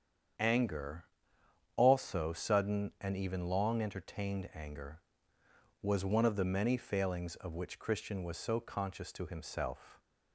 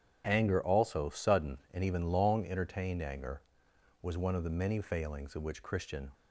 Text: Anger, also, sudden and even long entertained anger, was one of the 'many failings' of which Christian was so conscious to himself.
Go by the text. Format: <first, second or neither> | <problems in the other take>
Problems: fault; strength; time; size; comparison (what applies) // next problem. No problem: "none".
first | starts louder than the rest; strong; until 1.3 s; 9 dB; strong in the first // stops before "was so conscious to himself"; at 6.1 s